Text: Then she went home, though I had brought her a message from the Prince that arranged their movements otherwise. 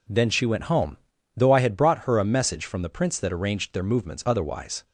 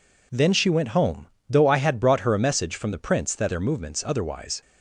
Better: first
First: none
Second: skips "arranged"; at 3.4 s

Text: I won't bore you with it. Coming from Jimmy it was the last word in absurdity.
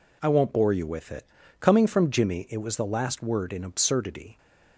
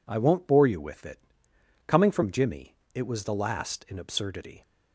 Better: first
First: none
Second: pauses between "Jimmy" and "it"; slight; at 2.7 s; 0.18 s long // skips "word"; at 3.8 s

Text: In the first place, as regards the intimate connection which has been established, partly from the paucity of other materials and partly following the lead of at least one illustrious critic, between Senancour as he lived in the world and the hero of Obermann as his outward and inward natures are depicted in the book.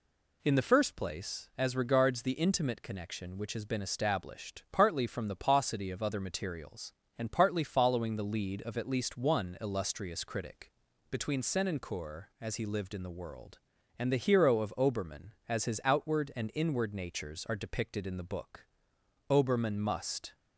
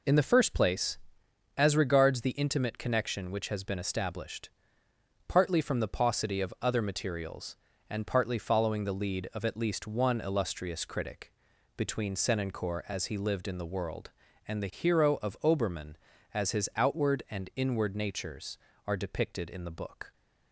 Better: second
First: goes on to say "Obermann must"; noticeable; from 19.3 s on; 1.0 s long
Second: none

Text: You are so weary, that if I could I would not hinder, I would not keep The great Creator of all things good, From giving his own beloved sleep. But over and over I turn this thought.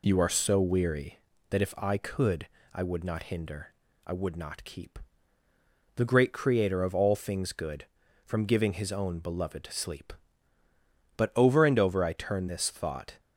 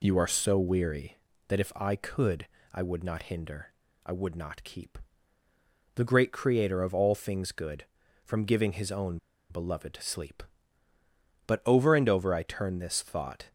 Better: first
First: pauses between "could" and "I"; slight; at 2.4 s; 0.26 s long // pauses between "keep" and "The"; noticeable; at 4.9 s; 0.96 s long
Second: pauses between "could" and "I"; slight; at 2.4 s; 0.26 s long // pauses between "keep" and "The"; noticeable; at 4.9 s; 0.96 s long // pauses between "own" and "beloved"; slight; at 9.1 s; 0.31 s long

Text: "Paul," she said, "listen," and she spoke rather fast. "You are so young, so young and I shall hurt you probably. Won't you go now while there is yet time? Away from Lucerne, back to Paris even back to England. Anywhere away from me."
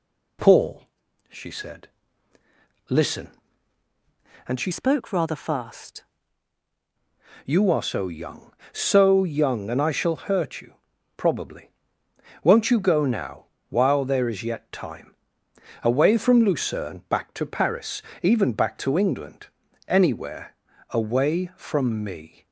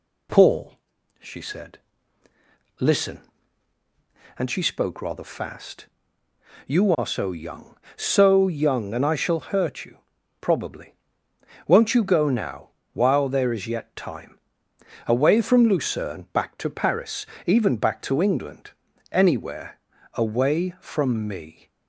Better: second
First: changes voice from "spoke" to "fast"; from 4.7 to 6.0 s; 1.3 s long // pauses between "you" and "probably"; at 10.7 s; 0.42 s long // pauses between "now" and "while"; slight; at 13.4 s; 0.22 s long // pauses between "Paris" and "even"; slight; at 18.0 s; 0.18 s long // pauses between "Anywhere" and "away"; at 20.5 s; 0.40 s long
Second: pauses between "you" and "probably"; at 9.9 s; 0.42 s long // pauses between "now" and "while"; slight; at 12.7 s; 0.22 s long // pauses between "Paris" and "even"; slight; at 17.2 s; 0.18 s long // pauses between "Anywhere" and "away"; at 19.7 s; 0.40 s long

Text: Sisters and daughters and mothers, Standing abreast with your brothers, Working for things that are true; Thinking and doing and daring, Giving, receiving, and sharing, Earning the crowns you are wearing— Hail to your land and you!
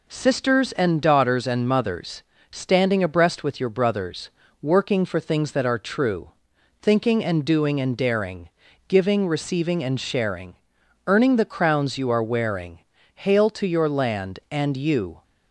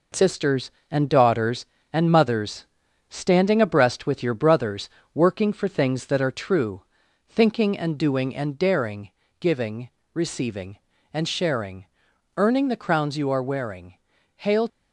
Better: first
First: none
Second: stops before "to your land and you"; at 14.6 s

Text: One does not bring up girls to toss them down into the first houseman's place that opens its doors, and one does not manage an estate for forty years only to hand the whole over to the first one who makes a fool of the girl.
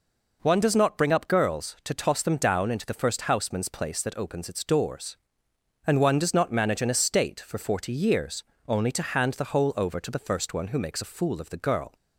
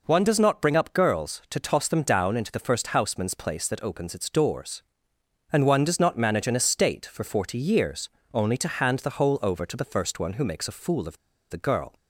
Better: first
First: pauses between "years" and "only"; slight; at 8.4 s; 0.20 s long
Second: pauses between "years" and "only"; slight; at 8.1 s; 0.20 s long // pauses between "of" and "the"; slight; at 11.1 s; 0.33 s long

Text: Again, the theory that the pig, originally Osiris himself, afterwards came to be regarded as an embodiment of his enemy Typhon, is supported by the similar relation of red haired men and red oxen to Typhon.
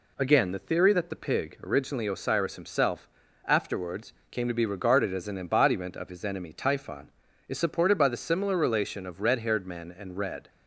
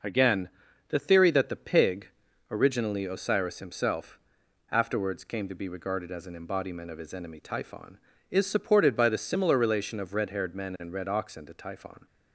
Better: second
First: pauses between "afterwards" and "came"; slight; at 4.1 s; 0.18 s long // stops before "oxen to Typhon"; at 10.4 s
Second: none

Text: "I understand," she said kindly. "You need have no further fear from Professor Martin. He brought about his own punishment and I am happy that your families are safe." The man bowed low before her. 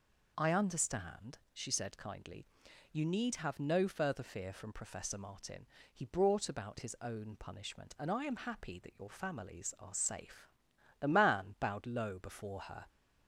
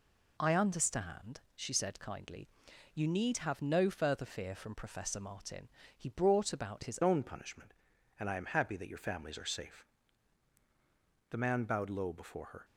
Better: first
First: none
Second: changes voice at "own"; from 7.0 s on; 5.6 s long

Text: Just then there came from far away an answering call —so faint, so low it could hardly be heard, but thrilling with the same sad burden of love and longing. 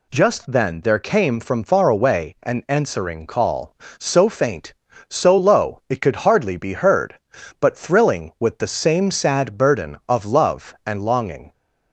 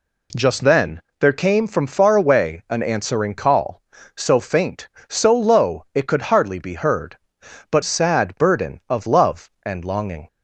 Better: first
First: none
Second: pauses between "then" and "there"; slight; at 1.0 s; 0.18 s long // skips "thrilling with the same"; at 7.8 s

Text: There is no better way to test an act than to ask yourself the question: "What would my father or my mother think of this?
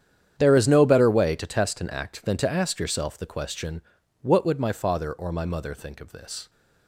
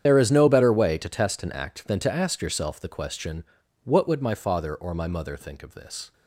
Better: first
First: starts louder than the rest; strong; until 1.4 s; 9 dB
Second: loses the start of "There"; at 0.0 s; 35 ms // starts louder than the rest; strong; until 1.0 s; 9 dB

